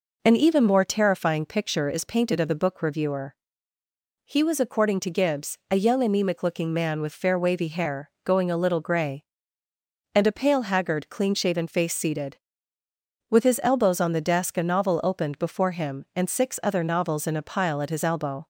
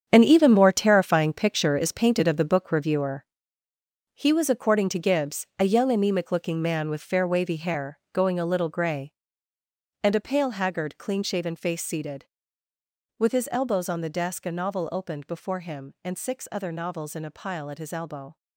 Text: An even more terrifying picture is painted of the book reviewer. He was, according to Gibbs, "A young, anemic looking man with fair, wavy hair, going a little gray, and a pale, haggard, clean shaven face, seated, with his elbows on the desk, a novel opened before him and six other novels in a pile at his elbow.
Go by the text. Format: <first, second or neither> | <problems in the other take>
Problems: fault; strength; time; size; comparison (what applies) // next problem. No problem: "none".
first | gets quieter; strong; throughout; 10.5 dB